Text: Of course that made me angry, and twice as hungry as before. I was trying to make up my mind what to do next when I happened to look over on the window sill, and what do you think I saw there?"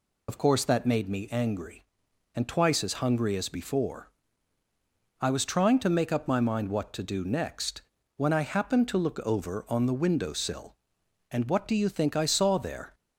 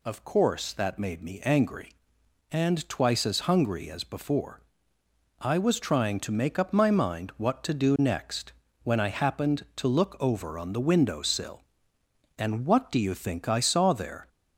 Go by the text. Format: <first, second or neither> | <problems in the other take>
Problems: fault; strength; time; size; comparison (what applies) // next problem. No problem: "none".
second | loses the start of "Of"; at 0.2 s; 75 ms // pauses between "next" and "when"; slight; at 7.8 s; 0.34 s long; slight in the second